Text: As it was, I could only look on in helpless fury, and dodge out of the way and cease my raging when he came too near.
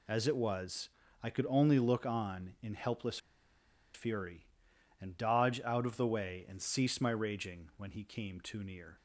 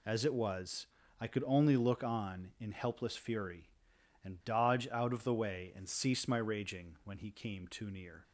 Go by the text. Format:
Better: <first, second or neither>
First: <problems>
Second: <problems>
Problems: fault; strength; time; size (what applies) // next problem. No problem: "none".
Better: second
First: pauses between "helpless" and "fury"; noticeable; at 3.1 s; 0.76 s long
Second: none